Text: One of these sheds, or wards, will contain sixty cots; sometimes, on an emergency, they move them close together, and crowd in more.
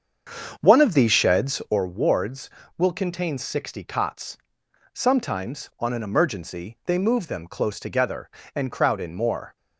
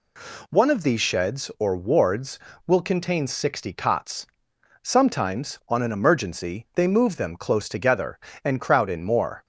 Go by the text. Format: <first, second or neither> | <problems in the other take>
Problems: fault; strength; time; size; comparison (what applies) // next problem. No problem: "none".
second | starts louder than the rest; until 1.8 s; 7 dB